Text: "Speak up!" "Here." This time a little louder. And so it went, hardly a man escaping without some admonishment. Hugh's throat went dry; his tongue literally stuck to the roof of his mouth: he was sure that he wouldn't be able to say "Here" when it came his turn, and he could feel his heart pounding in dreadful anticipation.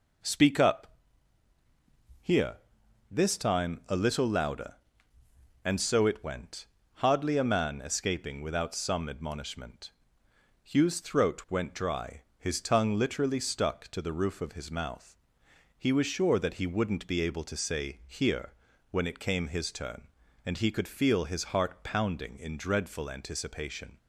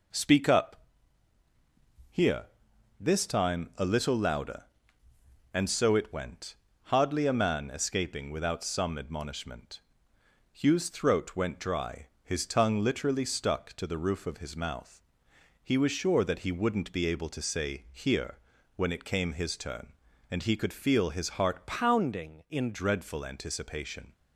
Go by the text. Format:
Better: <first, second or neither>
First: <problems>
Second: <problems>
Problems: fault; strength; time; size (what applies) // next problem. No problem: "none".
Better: first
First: pauses between "Here" and "when"; slight; at 18.5 s; 0.36 s long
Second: pauses between "Here" and "when"; slight; at 18.3 s; 0.36 s long // changes voice from "pounding" to "in"; from 21.6 to 22.7 s; 1.1 s long